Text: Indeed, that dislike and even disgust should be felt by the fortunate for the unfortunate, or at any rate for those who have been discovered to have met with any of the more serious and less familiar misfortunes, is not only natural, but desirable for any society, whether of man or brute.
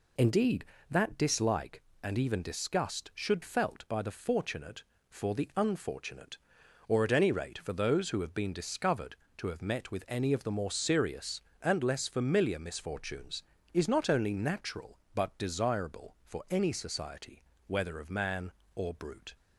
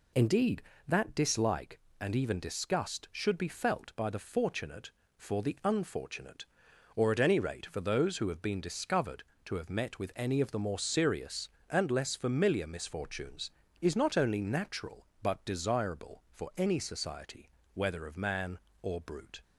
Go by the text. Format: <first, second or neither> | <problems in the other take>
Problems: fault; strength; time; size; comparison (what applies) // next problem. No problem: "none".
second | skips "be"; at 3.4 s